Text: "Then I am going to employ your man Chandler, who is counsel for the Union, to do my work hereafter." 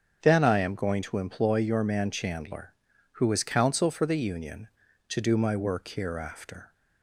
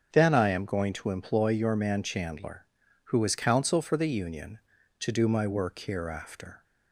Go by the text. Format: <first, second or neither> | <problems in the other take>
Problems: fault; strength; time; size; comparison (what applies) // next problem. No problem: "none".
neither | starts louder than the rest; strong; the same in both